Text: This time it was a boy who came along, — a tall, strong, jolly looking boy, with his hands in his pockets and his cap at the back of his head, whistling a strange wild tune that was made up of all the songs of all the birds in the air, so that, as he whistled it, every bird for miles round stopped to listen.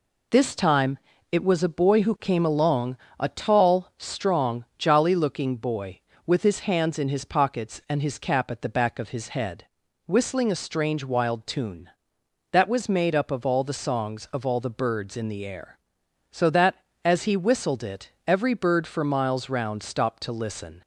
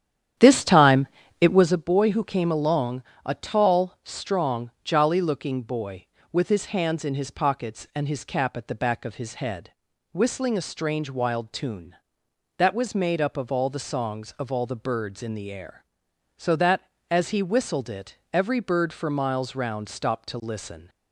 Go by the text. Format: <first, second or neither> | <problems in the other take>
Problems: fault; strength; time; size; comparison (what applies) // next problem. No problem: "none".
first | starts louder than the rest; strong; until 1.9 s; 10 dB // pauses between "time" and "it"; slight; at 1.0 s; 0.34 s long; slight in the first